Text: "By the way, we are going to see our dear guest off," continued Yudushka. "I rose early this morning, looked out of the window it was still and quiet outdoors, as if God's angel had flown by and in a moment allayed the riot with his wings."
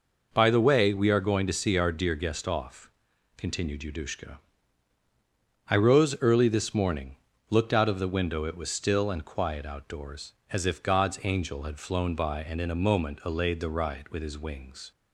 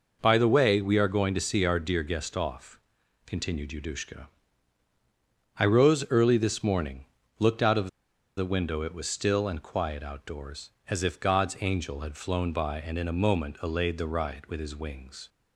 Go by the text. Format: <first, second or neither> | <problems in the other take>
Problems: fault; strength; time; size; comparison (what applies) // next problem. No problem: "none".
first | pauses between "of" and "the"; noticeable; at 7.8 s; 0.50 s long